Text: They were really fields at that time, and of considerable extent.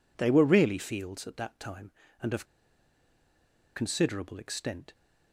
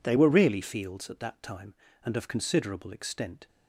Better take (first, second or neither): second